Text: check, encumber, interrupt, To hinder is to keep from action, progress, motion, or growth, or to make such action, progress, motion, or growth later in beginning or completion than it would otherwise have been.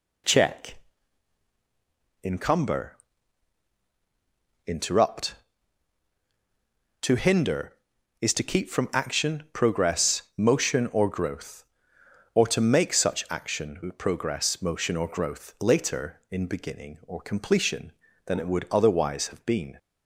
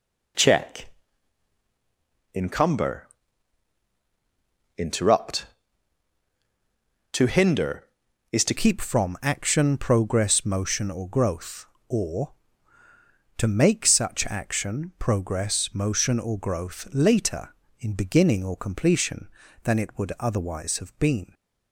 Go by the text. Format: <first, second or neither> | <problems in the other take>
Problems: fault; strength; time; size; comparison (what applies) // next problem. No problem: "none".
first | changes voice at "keep"; from 8.5 s on; 12.8 s long